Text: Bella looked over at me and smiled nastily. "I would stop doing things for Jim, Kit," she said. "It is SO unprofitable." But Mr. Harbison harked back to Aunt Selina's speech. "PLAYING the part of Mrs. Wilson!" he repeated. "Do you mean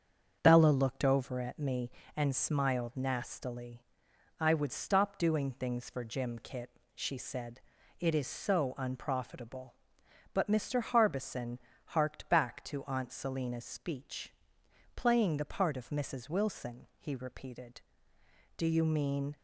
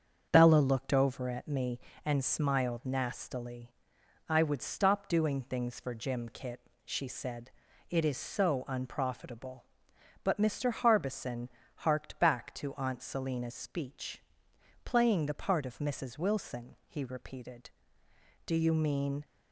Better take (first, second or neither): neither